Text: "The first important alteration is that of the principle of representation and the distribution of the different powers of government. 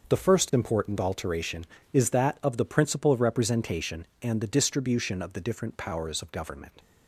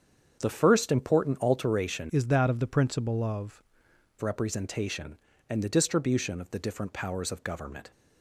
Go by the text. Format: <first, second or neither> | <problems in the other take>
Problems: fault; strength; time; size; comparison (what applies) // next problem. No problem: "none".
first | starts louder than the rest; strong; until 1.4 s; 7.5 dB // changes voice from "is" to "of"; from 2.1 to 3.6 s; 1.5 s long